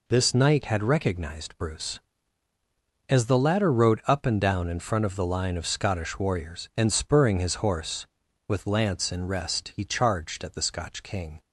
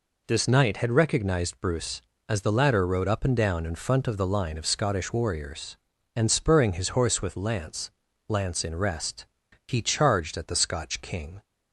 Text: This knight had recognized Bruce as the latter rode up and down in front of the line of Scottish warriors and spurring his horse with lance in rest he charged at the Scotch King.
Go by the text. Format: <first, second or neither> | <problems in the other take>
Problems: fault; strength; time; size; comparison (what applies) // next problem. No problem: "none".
first | says "lance" twice; at 8.2 s // pauses between "rest" and "he"; at 9.2 s; 0.42 s long